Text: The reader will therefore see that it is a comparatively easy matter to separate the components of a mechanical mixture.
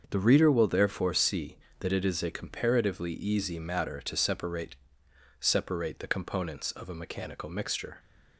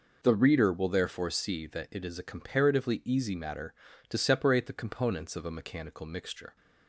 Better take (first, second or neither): second